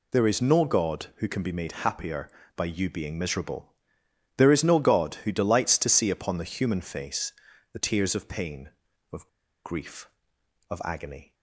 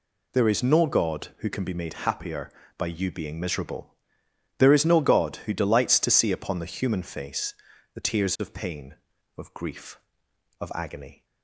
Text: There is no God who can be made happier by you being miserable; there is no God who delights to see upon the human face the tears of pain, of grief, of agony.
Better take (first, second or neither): second